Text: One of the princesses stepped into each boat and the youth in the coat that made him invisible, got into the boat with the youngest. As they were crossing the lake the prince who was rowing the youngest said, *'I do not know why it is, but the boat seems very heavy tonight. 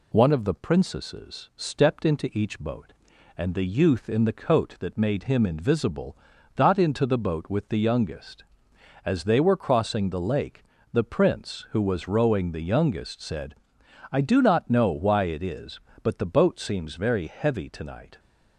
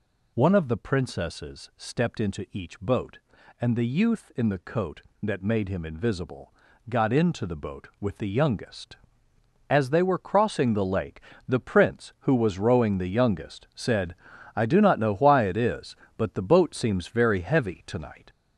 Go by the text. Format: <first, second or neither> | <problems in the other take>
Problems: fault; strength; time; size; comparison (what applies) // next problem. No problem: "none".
first | gets louder; noticeable; throughout; 4.5 dB // pauses between "lake" and "the"; slight; at 11.1 s; 0.30 s long; slight in the first